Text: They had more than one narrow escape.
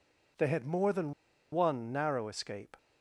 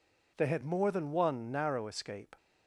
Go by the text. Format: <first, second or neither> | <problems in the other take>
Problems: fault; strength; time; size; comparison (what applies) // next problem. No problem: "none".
second | pauses between "than" and "one"; at 1.1 s; 0.39 s long